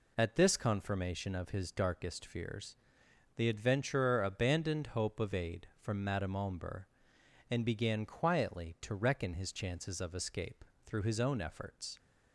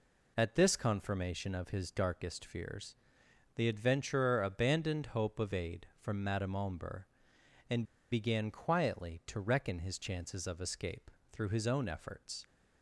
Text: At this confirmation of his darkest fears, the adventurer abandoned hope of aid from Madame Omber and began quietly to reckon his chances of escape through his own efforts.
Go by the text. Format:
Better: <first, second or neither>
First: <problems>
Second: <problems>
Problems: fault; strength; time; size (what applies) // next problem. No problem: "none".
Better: first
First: pauses between "escape" and "through"; slight; at 10.6 s; 0.22 s long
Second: pauses between "and" and "began"; slight; at 7.8 s; 0.27 s long // pauses between "escape" and "through"; slight; at 11.0 s; 0.22 s long